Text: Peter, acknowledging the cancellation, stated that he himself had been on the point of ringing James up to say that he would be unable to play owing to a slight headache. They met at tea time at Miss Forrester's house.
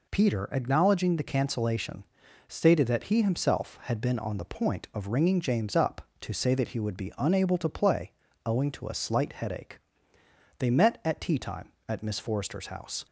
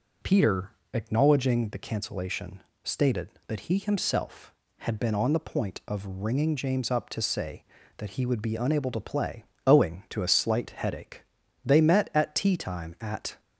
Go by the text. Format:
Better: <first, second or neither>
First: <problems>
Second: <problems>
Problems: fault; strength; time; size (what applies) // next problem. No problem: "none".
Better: first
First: pauses between "play" and "owing"; slight; at 8.1 s; 0.32 s long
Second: pauses between "play" and "owing"; slight; at 9.4 s; 0.22 s long // stops before "Miss Forrester's house"; at 13.3 s